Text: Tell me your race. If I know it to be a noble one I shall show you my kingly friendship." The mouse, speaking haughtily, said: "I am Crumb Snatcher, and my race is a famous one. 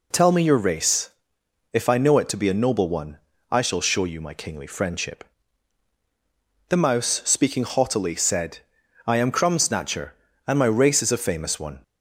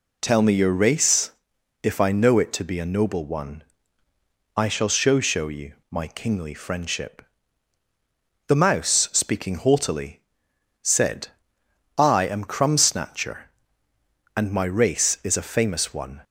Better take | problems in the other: first | pauses between "one" and "I"; noticeable; at 3.6 s; 0.94 s long; slight in the first // says "show" twice; at 5.2 s // pauses between "you" and "my"; slight; at 5.7 s; 0.16 s long

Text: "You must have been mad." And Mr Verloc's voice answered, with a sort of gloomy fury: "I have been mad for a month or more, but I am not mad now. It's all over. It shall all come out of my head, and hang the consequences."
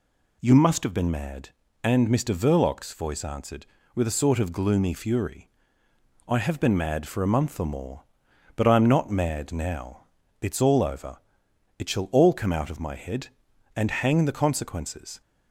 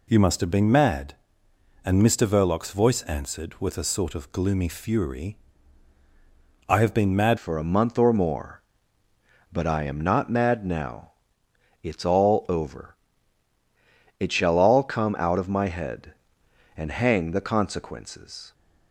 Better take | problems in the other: first | changes voice at "for"; from 7.3 s on; 11.2 s long

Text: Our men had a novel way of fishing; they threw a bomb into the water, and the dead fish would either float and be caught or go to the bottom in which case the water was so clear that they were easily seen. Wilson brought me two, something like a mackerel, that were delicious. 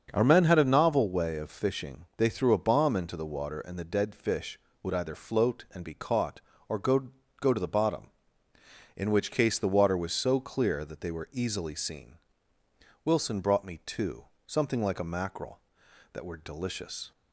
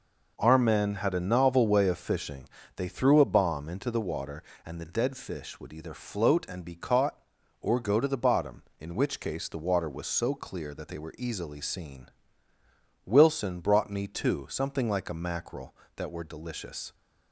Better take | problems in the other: second | starts louder than the rest; until 1.1 s; 6.5 dB // says "go" twice; at 7.4 s

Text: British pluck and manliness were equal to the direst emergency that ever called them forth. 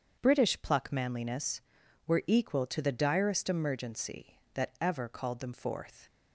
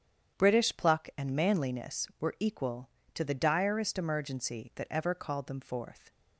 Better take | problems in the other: second | starts louder than the rest; strong; until 1.2 s; 7.5 dB; strong in the second // skips "and"; at 0.9 s

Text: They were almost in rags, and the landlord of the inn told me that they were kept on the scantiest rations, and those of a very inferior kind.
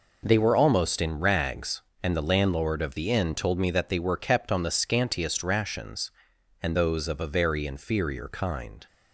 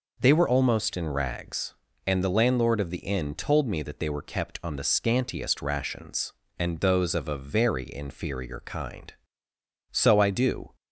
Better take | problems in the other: first | goes on to say "So I do"; noticeable; from 9.9 s on; 0.84 s long

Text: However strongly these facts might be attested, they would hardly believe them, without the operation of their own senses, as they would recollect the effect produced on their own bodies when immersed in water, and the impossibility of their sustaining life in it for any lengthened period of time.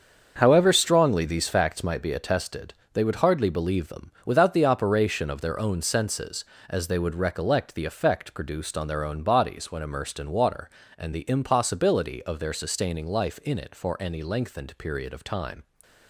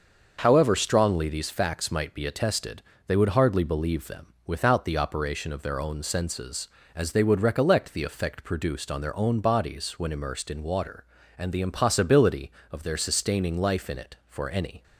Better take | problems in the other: first | starts louder than the rest; until 1.4 s; 6 dB; also in the first // stops before "lengthened period of time"; at 14.8 s

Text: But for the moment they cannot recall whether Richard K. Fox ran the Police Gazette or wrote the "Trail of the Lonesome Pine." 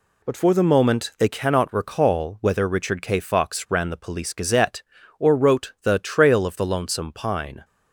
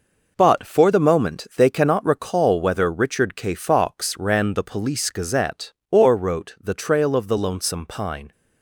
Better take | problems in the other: neither | none

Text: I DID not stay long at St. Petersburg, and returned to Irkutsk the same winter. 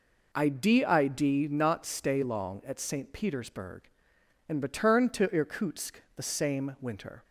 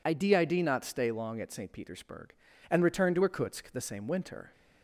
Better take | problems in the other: neither | none

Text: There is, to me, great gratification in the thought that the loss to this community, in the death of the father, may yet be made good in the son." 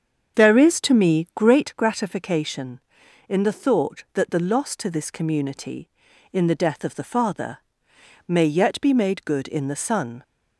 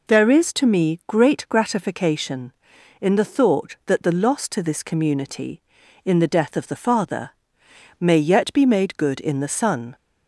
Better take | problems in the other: second | starts louder than the rest; strong; until 1.6 s; 7.5 dB

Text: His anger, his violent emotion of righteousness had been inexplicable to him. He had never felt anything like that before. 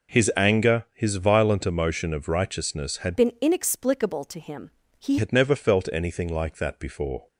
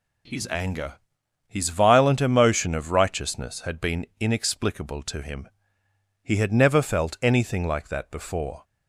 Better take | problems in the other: second | changes voice from "been" to "He"; from 3.1 to 5.1 s; 2.0 s long

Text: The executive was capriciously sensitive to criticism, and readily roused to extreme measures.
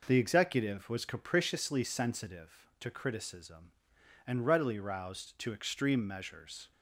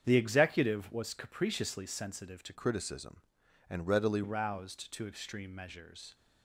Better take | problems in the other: first | starts louder than the rest; strong; until 1.0 s; 8 dB // changes voice from "criticism" to "readily"; from 2.5 to 4.2 s; 1.7 s long

